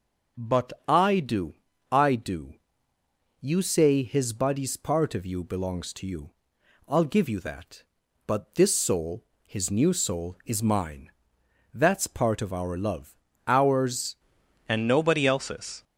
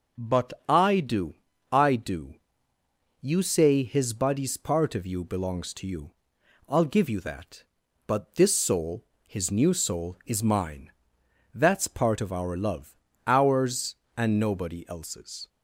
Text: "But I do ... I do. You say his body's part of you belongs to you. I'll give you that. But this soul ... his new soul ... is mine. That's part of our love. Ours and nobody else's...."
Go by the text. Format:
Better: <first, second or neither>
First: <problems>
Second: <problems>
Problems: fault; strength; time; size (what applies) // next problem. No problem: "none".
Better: second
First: pauses between "But" and "I"; slight; at 0.7 s; 0.16 s long // changes voice at "and"; from 14.6 s on; 1.2 s long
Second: pauses between "But" and "I"; slight; at 0.5 s; 0.16 s long